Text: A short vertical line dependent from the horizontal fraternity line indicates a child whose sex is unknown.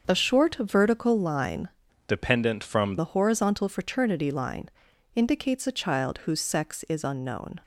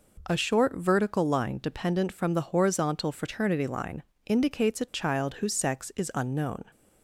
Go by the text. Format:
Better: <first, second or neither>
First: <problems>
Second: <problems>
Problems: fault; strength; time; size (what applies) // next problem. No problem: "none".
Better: second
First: starts louder than the rest; until 1.1 s; 7 dB // changes voice from "dependent" to "from"; from 2.0 to 2.9 s; 0.9 s long // pauses between "line" and "indicates"; noticeable; at 4.6 s; 0.46 s long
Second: pauses between "line" and "indicates"; slight; at 4.0 s; 0.24 s long